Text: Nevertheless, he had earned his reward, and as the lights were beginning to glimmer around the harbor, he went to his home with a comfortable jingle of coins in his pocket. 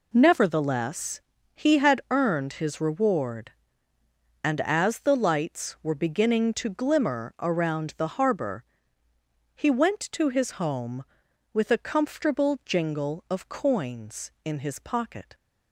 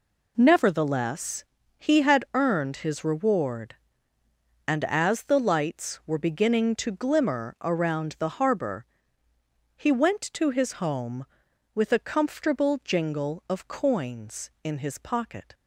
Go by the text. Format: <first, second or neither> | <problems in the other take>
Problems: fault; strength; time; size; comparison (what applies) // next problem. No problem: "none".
neither | none